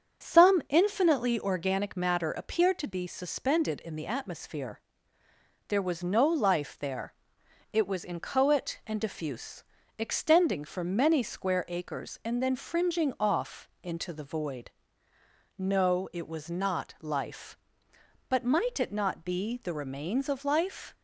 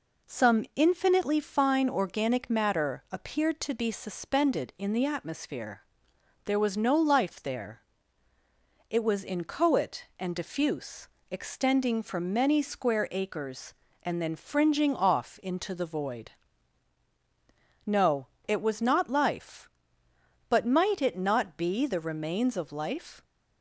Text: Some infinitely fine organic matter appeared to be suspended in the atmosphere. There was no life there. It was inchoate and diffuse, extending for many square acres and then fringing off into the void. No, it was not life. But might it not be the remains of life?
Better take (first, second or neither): second